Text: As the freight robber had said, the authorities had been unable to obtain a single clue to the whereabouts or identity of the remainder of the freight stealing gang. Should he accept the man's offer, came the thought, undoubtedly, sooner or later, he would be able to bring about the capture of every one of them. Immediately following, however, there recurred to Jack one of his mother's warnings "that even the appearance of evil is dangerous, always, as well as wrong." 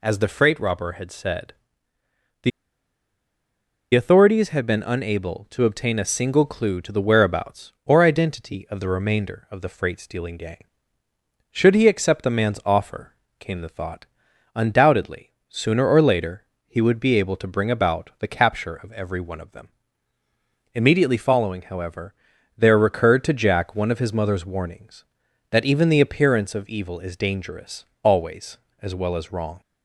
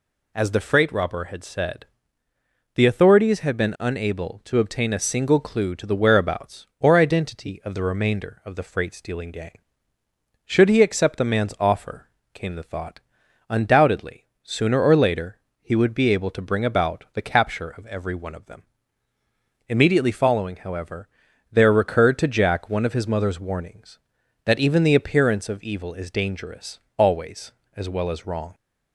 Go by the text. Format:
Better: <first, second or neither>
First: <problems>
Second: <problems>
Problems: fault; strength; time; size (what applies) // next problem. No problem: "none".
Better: second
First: pauses between "the" and "authorities"; strong; at 2.5 s; 1.4 s long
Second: none